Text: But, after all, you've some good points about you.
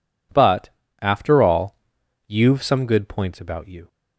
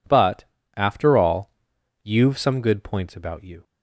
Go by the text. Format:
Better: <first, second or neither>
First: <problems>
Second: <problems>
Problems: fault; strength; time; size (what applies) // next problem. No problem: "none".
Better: neither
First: none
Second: none